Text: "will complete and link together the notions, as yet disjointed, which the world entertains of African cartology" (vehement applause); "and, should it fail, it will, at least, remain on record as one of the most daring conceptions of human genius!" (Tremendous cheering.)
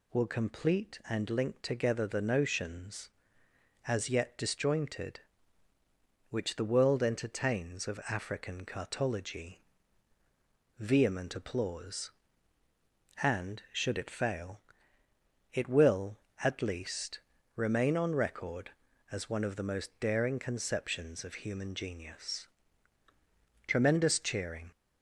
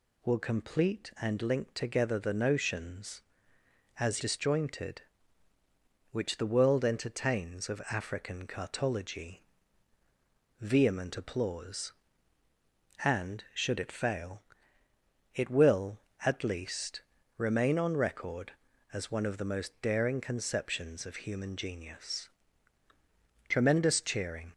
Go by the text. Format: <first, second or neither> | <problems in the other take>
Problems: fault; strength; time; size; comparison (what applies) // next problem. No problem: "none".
first | skips "yet"; at 4.2 s